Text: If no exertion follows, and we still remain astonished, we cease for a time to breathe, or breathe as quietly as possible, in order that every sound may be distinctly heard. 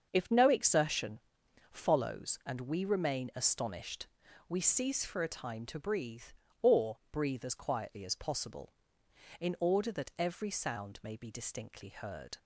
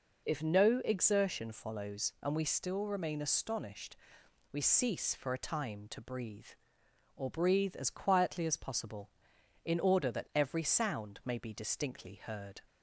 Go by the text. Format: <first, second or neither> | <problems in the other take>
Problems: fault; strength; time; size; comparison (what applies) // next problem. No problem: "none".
second | starts louder than the rest; until 1.1 s; 7 dB // pauses between "exertion" and "follows"; noticeable; at 1.1 s; 0.50 s long // skips "still"; at 2.8 s